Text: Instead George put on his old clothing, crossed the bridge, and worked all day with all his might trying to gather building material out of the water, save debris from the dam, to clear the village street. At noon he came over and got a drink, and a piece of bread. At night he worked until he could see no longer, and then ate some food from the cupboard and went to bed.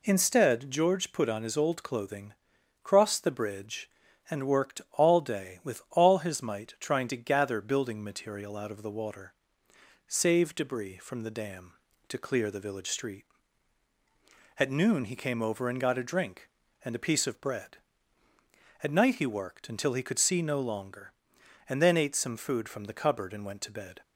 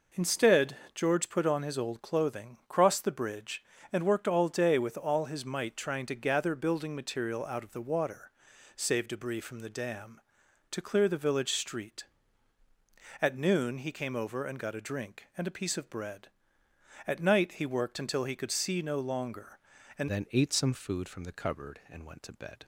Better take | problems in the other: first | pauses between "Instead" and "George"; slight; at 0.7 s; 0.18 s long // changes voice at "then"; from 20.0 s on; 2.6 s long

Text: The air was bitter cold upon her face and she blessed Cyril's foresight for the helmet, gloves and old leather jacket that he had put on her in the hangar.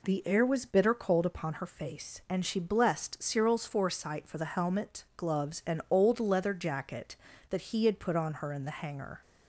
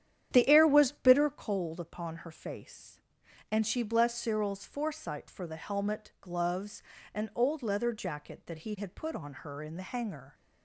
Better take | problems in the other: first | starts louder than the rest; strong; until 1.5 s; 9.5 dB

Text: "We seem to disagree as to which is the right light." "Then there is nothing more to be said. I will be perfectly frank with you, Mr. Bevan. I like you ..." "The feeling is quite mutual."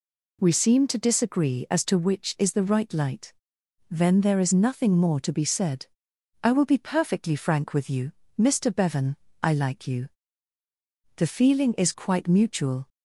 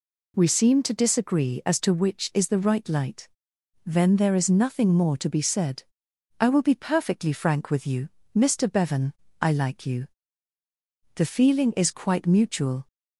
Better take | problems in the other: neither | none

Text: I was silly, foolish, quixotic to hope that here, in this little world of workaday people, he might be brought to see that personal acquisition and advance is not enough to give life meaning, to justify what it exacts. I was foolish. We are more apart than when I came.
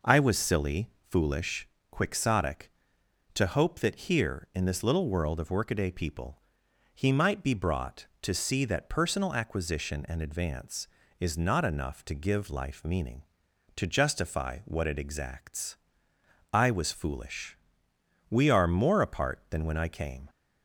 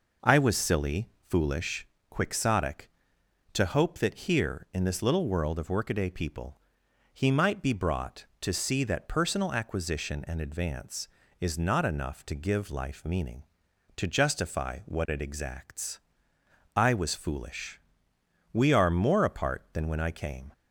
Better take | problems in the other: neither | none

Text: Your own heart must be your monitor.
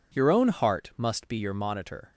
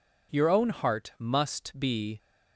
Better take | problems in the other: first | stops before "your monitor"; at 2.1 s

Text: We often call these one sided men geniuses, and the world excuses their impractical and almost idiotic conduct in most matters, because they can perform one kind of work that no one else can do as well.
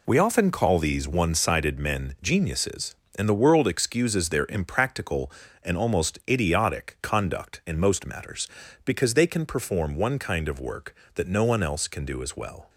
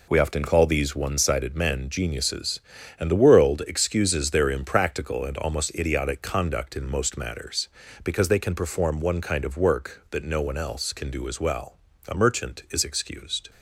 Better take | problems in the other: first | goes on to say "A merchant is excused"; from 12.0 s on; 1.4 s long

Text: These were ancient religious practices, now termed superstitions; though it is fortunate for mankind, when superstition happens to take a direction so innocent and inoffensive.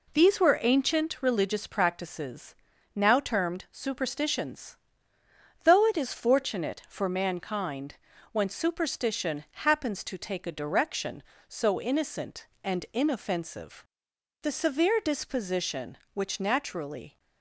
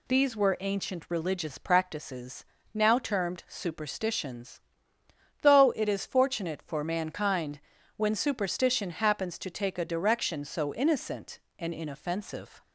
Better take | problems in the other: second | goes on to say "The severe disposition which naturally"; strong; from 14.4 s on; 2.7 s long

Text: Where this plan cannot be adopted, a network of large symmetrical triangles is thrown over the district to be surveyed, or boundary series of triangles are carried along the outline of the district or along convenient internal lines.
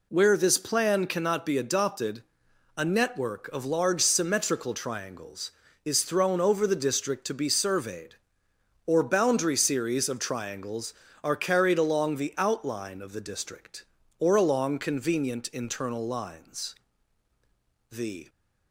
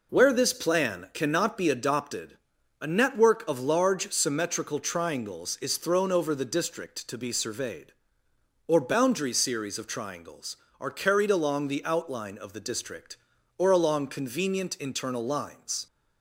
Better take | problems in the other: second | goes on to say "The"; slight; from 17.9 s on; 0.38 s long

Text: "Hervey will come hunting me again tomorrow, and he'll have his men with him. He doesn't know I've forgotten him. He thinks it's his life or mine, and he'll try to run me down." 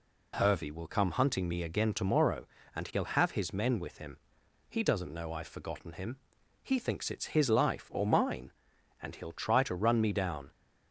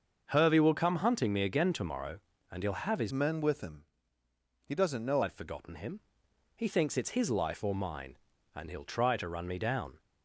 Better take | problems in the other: first | starts louder than the rest; until 1.3 s; 6.5 dB // changes voice from "men" to "know"; from 3.1 to 5.2 s; 2.1 s long

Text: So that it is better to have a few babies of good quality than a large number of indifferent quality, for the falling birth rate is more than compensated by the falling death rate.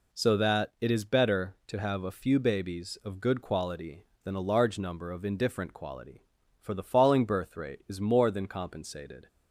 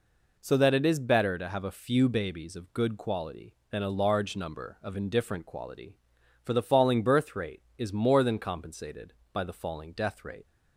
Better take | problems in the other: second | stops before "by the falling death rate"; at 9.2 s

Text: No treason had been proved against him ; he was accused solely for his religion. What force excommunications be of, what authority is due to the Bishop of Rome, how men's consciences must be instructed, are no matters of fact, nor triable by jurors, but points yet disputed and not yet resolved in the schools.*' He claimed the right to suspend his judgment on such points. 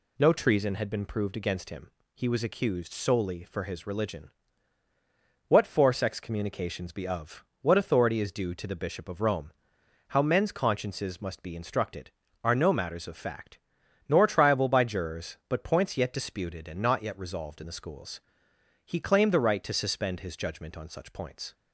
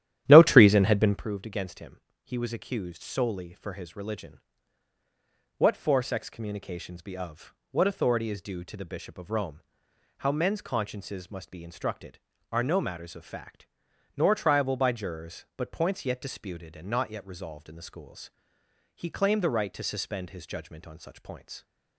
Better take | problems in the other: first | starts louder than the rest; strong; until 1.3 s; 12 dB

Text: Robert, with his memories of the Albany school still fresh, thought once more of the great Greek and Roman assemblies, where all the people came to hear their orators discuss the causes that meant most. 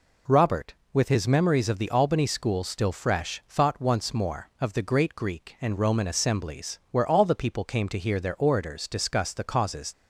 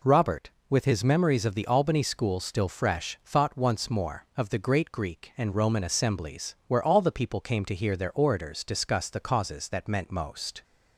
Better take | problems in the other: second | stops before "that meant most"; at 9.9 s

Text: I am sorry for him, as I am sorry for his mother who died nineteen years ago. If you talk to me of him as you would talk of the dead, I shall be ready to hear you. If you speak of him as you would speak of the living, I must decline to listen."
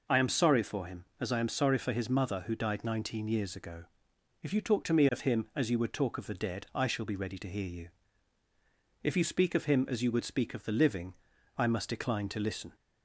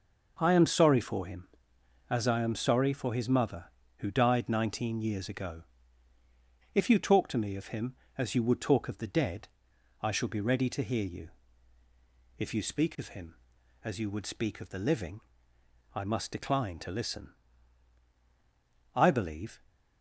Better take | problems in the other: first | goes on to say "I believe"; noticeable; from 18.9 s on; 0.64 s long

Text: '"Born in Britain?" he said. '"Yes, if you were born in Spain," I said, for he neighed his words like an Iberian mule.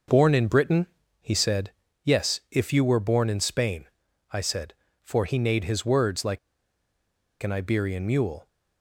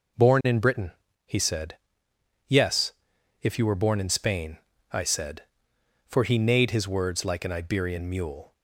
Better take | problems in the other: second | pauses between "like" and "an"; at 6.3 s; 1.0 s long

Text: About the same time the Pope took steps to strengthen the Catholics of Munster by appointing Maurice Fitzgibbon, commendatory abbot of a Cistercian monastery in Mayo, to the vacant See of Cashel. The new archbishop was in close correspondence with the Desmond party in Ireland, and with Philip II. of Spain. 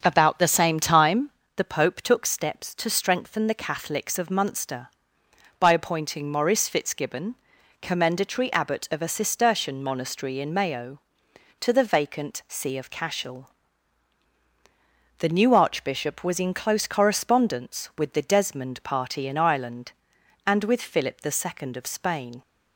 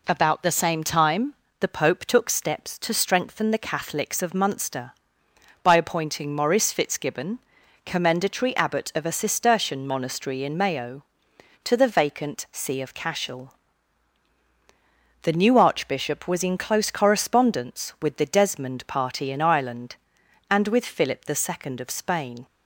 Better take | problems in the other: second | starts louder than the rest; until 1.4 s; 7 dB // pauses between "time" and "the"; slight; at 1.2 s; 0.28 s long; slight in the second

